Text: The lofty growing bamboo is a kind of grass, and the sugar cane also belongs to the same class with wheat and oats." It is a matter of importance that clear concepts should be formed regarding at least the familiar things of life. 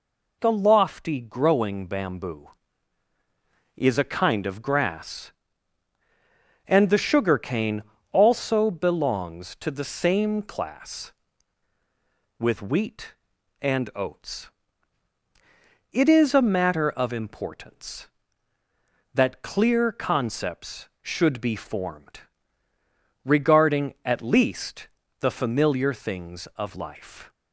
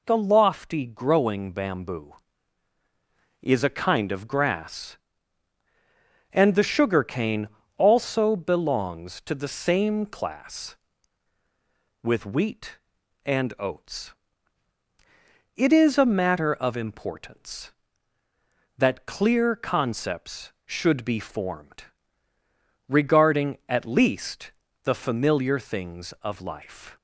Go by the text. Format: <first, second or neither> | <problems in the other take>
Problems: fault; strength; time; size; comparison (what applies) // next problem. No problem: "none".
neither | pauses between "cane" and "also"; slight; the same in both // pauses between "formed" and "regarding"; the same in both // pauses between "least" and "the"; slight; the same in both